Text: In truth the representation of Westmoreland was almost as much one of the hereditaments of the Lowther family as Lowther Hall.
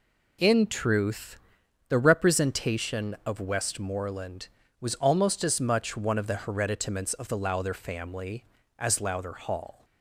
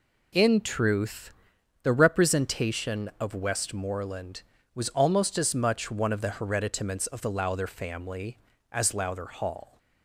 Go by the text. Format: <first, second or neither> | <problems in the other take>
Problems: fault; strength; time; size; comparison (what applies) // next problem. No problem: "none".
neither | pauses between "truth" and "the"; noticeable; the same in both